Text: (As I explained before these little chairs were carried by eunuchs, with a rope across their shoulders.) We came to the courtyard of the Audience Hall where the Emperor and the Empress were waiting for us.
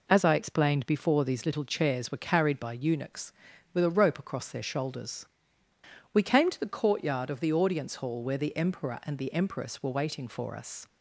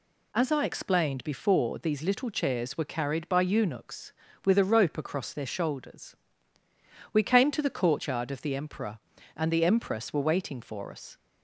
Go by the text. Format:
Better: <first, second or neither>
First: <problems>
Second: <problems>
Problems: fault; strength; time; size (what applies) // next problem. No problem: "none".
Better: first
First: none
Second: skips "Audience Hall where the"; at 8.5 s